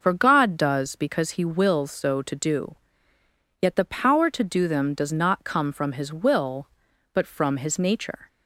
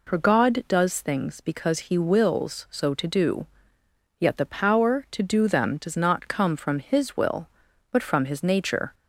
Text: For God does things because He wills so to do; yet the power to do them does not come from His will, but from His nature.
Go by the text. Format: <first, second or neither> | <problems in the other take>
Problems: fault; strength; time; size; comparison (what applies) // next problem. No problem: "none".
second | skips "things"; at 0.9 s